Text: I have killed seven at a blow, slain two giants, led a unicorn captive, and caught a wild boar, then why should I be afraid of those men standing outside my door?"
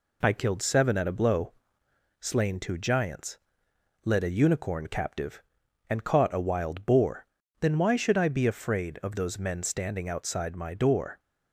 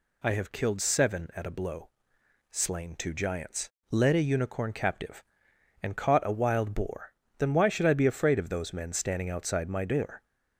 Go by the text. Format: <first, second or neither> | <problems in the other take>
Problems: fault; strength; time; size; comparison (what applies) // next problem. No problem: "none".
second | skips "have"; at 0.3 s